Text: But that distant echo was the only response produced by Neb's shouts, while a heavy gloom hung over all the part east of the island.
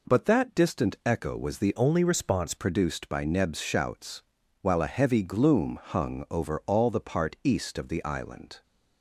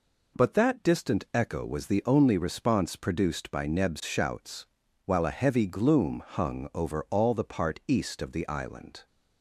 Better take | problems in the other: second | changes voice from "only" to "response"; from 1.7 to 2.5 s; 0.8 s long

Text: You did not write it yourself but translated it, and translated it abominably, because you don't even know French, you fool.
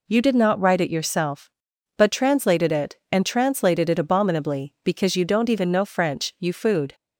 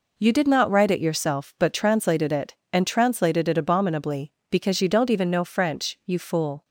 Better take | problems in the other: second | says "food" for "fool"; at 6.5 s

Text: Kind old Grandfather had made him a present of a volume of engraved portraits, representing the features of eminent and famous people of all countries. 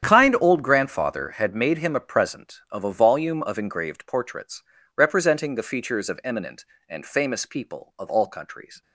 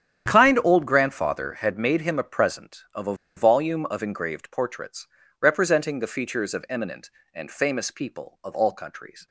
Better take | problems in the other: first | starts louder than the rest; strong; until 1.3 s; 9.5 dB; strong in the first // pauses between "a" and "volume"; slight; at 3.1 s; 0.21 s long

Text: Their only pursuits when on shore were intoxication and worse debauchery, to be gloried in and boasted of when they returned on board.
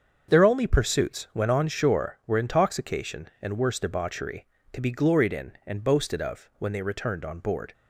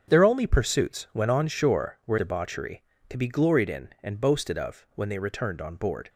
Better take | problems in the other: first | starts louder than the rest; until 1.1 s; 7 dB; also in the first // skips "intoxication and worse"; at 2.1 s

